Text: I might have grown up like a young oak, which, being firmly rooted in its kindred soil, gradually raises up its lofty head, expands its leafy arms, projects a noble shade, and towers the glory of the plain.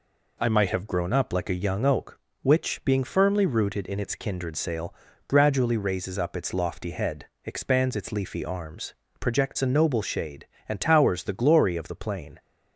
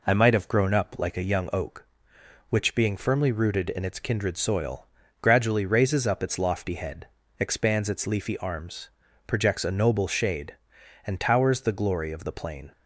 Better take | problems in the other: second | says "sail" for "soil"; at 4.5 s

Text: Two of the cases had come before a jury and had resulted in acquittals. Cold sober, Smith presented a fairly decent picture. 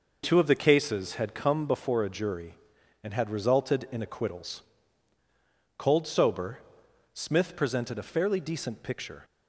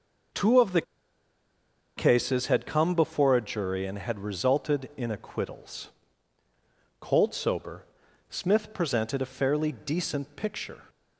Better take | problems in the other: first | pauses between "the" and "cases"; at 0.8 s; 1.1 s long

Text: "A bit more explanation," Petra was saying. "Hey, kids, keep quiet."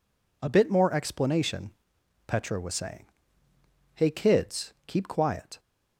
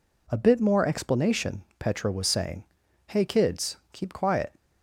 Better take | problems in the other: neither | none

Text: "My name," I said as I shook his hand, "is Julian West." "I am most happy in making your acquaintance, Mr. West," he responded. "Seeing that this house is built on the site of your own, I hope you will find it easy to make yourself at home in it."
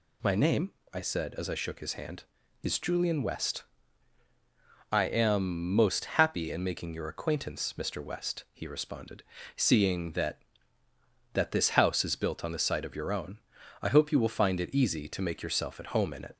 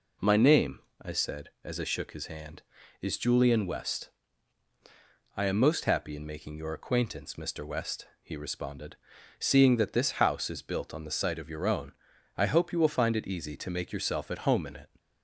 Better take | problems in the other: second | says "that" twice; at 11.3 s

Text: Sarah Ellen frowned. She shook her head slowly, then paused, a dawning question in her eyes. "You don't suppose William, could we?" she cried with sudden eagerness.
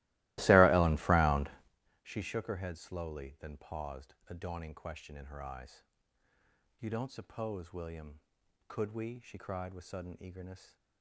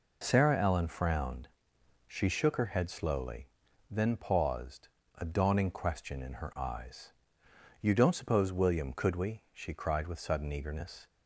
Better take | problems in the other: second | starts louder than the rest; strong; until 1.7 s; 19 dB

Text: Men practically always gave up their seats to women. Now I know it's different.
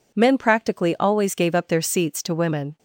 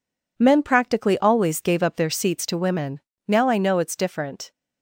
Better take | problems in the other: second | stops before "Now I know it's different"; at 2.7 s

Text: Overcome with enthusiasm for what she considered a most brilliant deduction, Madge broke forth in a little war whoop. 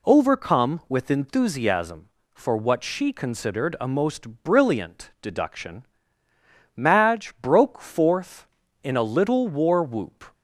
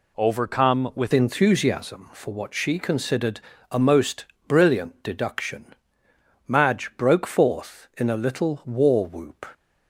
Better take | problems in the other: first | changes voice at "enthusiasm"; from 1.1 s on; 8.3 s long // pauses between "considered" and "a"; slight; at 3.3 s; 0.32 s long // pauses between "most" and "brilliant"; slight; at 4.2 s; 0.22 s long

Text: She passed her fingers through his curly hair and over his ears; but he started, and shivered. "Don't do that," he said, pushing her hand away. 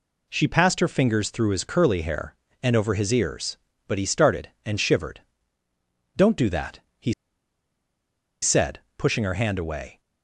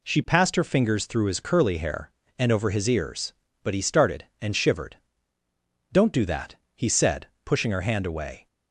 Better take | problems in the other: second | pauses between "he" and "said"; strong; at 7.1 s; 1.2 s long

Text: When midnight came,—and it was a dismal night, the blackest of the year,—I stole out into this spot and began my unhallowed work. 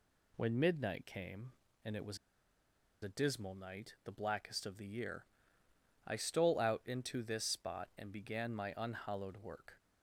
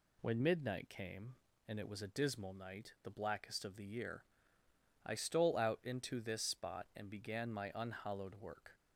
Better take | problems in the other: second | pauses between "was" and "a"; noticeable; at 2.1 s; 0.86 s long

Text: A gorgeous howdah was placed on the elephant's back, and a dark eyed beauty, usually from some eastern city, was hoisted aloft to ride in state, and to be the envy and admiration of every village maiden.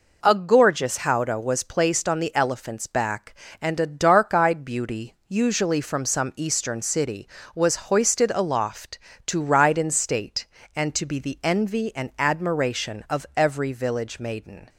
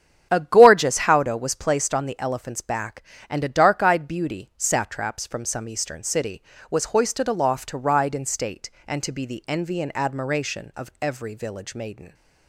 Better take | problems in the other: first | starts louder than the rest; strong; until 1.3 s; 8.5 dB // says "satraps" for "usually"; at 4.5 s

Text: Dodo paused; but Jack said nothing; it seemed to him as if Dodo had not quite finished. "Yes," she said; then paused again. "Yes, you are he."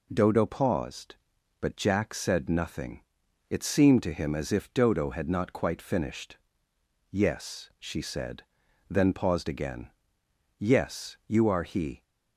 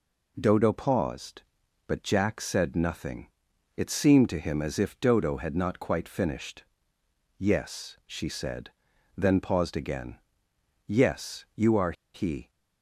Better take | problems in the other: first | pauses between "are" and "he"; slight; at 11.9 s; 0.21 s long

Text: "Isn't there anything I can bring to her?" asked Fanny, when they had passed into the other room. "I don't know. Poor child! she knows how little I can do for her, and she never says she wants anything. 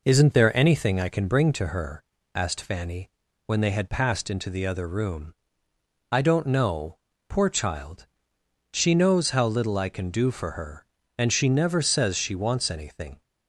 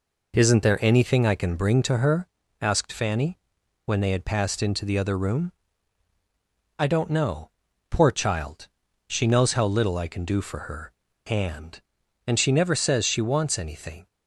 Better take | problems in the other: first | says "and" twice; at 12.2 s

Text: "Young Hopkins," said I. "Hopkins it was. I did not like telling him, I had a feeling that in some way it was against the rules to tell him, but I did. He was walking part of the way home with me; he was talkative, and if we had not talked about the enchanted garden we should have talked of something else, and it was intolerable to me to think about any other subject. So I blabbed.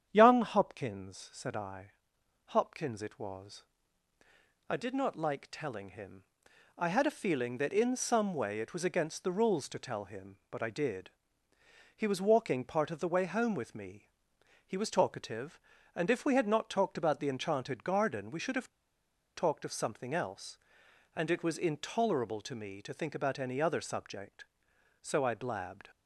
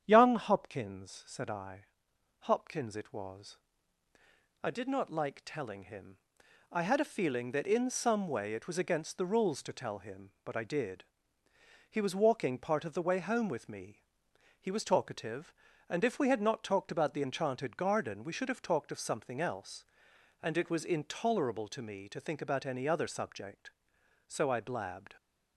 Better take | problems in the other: second | starts louder than the rest; strong; until 1.1 s; 9 dB; strong in the second // pauses between "have" and "talked"; noticeable; at 18.6 s; 0.66 s long

